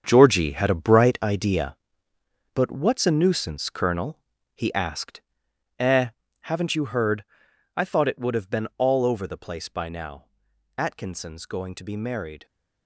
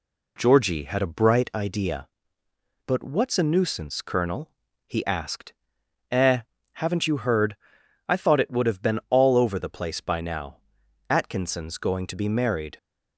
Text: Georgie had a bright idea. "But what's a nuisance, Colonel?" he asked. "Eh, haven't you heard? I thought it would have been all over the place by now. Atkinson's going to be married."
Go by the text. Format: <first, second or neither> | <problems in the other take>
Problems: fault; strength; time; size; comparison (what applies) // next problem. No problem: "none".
second | gets quieter; strong; throughout; 11 dB